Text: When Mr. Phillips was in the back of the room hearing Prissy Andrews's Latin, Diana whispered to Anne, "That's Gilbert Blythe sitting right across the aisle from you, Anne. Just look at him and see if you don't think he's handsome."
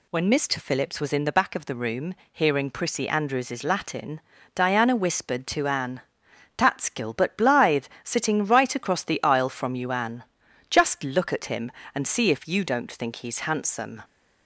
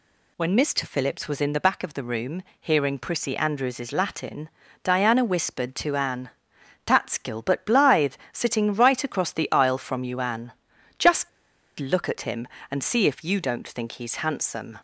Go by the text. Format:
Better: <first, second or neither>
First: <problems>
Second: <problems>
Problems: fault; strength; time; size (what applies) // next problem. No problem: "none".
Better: first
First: pauses between "room" and "hearing"; slight; at 2.1 s; 0.18 s long // pauses between "Blythe" and "sitting"; slight; at 7.8 s; 0.16 s long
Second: pauses between "room" and "hearing"; slight; at 2.4 s; 0.18 s long // pauses between "Blythe" and "sitting"; slight; at 8.1 s; 0.16 s long // pauses between "Just" and "look"; noticeable; at 11.2 s; 0.49 s long